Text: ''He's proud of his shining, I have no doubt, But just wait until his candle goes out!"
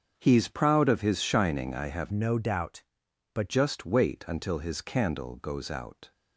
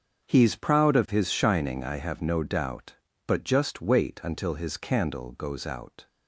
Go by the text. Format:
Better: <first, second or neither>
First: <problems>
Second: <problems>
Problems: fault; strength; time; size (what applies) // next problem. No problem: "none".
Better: second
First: starts louder than the rest; strong; until 1.1 s; 7 dB // changes voice from "no" to "But"; from 2.1 to 3.5 s; 1.4 s long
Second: starts louder than the rest; strong; until 1.3 s; 7 dB